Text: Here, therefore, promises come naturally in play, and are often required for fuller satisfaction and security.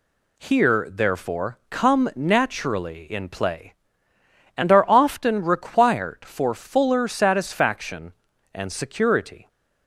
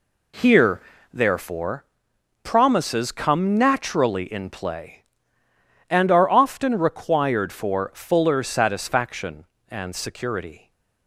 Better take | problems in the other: second | skips "promises"; at 1.6 s

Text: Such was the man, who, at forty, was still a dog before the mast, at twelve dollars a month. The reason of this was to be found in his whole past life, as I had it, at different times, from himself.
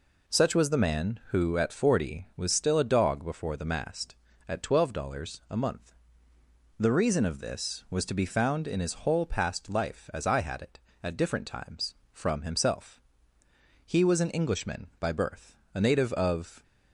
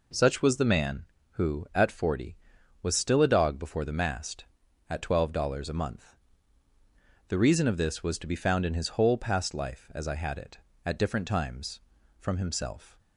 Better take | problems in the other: second | goes on to say "He was an Englishman by birth a native of"; strong; from 13.8 s on; 2.7 s long

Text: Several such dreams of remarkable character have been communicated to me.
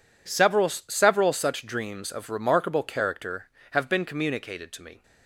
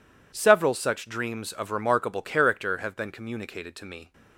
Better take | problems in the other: second | says "Several" twice; at 0.6 s

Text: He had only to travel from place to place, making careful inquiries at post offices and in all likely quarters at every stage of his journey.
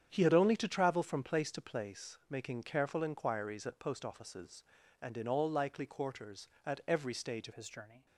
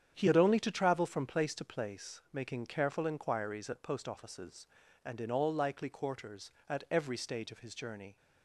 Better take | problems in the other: second | starts louder than the rest; strong; until 1.1 s; 8.5 dB; strong in the second // changes voice at "his"; from 7.5 s on; 0.5 s long

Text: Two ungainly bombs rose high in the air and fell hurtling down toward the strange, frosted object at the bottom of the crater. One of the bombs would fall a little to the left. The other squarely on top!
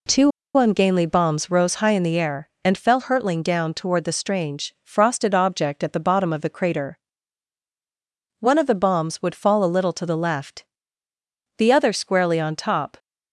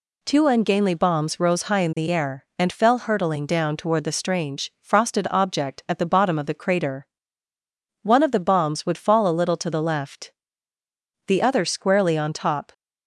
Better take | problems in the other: second | pauses between "Two" and "ungainly"; slight; at 0.3 s; 0.26 s long

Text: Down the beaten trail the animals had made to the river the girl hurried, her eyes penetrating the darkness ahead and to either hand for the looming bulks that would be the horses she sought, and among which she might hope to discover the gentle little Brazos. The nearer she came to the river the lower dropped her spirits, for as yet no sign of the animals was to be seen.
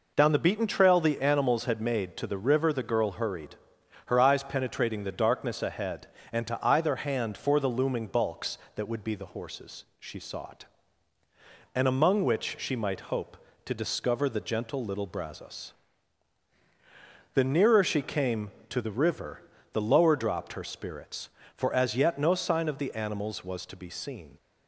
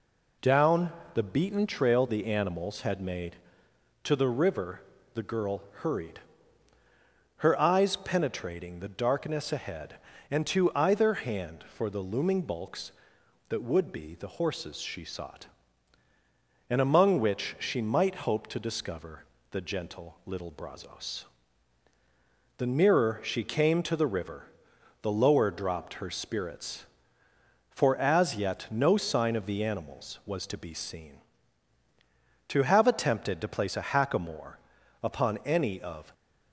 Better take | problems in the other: first | pauses between "Down" and "the"; slight; at 0.9 s; 0.22 s long // pauses between "river" and "the"; slight; at 4.8 s; 0.32 s long // pauses between "girl" and "hurried"; slight; at 5.6 s; 0.18 s long // pauses between "discover" and "the"; slight; at 19.2 s; 0.26 s long // pauses between "river" and "the"; noticeable; at 24.4 s; 0.56 s long; slight in the first // goes on to say "To have attempted to place a hackamore upon any of"; strong; from 32.4 s on; 3.6 s long

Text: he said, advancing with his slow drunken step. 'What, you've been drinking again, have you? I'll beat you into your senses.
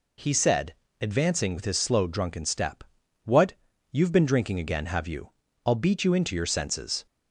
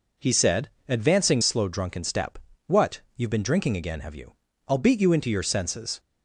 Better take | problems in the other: first | skips "with his"; at 1.4 s

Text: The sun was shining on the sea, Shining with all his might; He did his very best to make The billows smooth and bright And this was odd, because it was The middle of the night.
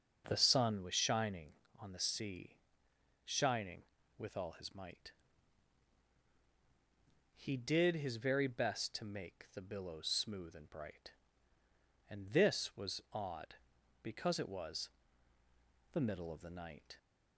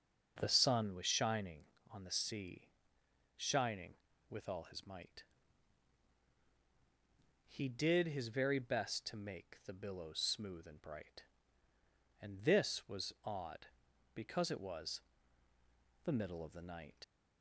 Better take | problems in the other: first | pauses between "was" and "The"; at 15.0 s; 1.0 s long; also in the first // leaves "night" unfinished; at 17.0 s; 50 ms

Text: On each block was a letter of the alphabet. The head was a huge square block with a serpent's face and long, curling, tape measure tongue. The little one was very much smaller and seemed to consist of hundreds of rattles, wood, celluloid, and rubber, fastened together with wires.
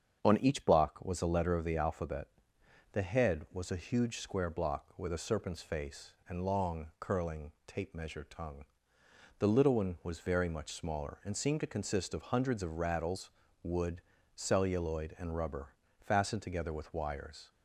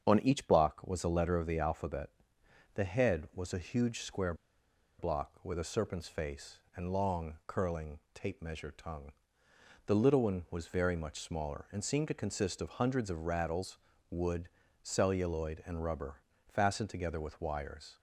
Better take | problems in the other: first | starts louder than the rest; strong; until 1.1 s; 7.5 dB; strong in the first // pauses between "square" and "block"; noticeable; at 4.3 s; 0.65 s long

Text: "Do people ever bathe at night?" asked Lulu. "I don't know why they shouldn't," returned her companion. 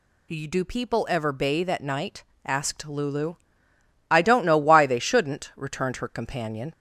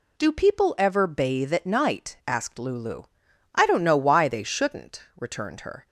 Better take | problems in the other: first | stops before "companion"; at 5.8 s

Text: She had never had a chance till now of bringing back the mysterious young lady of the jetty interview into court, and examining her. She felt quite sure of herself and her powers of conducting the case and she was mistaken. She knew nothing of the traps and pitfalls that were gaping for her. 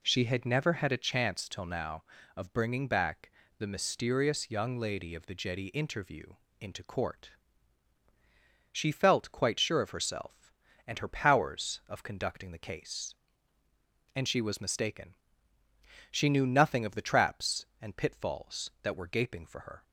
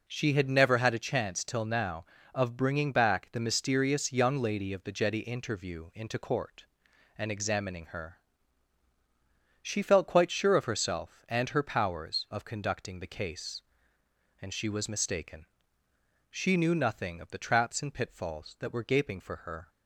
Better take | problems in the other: second | pauses between "back" and "the"; slight; at 3.3 s; 0.28 s long // pauses between "interview" and "into"; slight; at 6.3 s; 0.26 s long // skips "and examining her"; at 8.0 s

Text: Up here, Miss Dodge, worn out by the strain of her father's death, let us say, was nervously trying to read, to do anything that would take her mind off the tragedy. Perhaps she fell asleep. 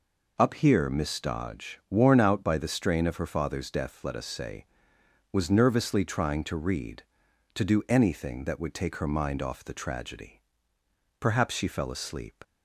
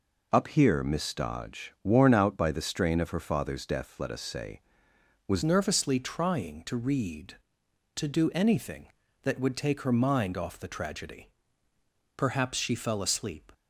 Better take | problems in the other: first | changes voice at "nervously"; from 5.4 s on; 8.1 s long

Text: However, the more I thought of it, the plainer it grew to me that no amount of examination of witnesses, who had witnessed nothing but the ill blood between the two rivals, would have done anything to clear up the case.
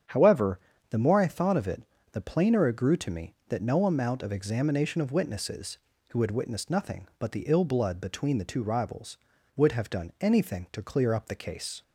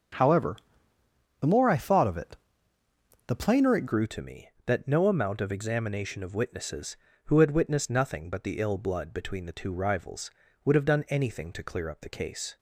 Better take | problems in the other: first | starts louder than the rest; until 1.9 s; 7 dB; strong in the first // changes voice at "grew"; from 3.8 s on; 8.7 s long

